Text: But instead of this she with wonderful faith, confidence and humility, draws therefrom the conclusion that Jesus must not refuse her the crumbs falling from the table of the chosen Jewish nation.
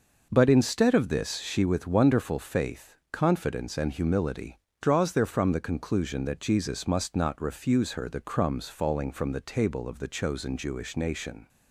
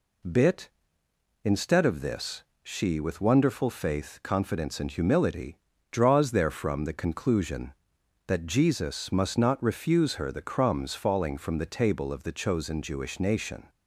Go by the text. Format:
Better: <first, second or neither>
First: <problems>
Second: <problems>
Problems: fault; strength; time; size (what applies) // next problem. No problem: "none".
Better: first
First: none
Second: says "Bit" for "But"; at 0.2 s // pauses between "this" and "she"; slight; at 2.4 s; 0.18 s long